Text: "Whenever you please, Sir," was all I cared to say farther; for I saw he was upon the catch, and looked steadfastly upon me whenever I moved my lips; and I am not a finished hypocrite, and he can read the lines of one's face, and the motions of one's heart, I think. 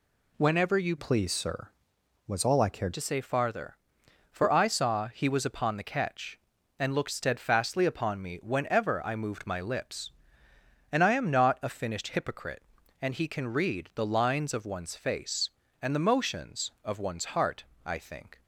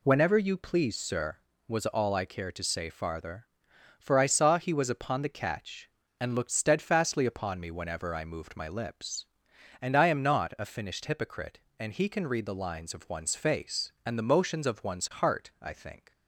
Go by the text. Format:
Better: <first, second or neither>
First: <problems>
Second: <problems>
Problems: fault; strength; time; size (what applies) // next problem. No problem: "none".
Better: second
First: changes voice from "please" to "cared"; from 0.9 to 2.9 s; 2.0 s long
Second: none